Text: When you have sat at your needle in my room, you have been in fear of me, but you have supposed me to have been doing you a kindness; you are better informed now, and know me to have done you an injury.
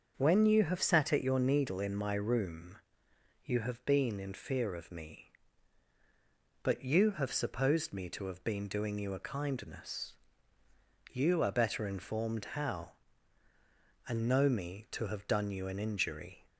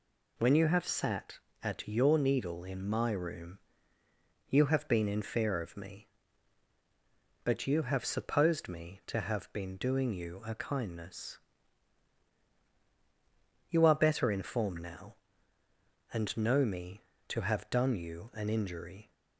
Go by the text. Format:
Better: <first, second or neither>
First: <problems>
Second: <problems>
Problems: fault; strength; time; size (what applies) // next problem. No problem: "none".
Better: second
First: starts louder than the rest; until 1.1 s; 6.5 dB // says "how" for "now"; at 12.5 s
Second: none